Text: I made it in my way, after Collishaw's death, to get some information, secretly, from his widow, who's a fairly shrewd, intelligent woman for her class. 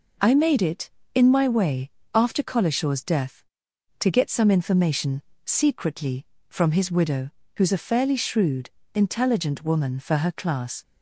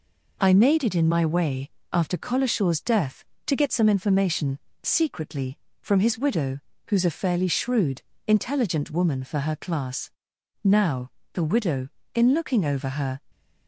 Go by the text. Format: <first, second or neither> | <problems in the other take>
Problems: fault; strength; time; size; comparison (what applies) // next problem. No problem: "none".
first | goes on to say "Now the widow in looking over her"; strong; from 10.6 s on; 2.5 s long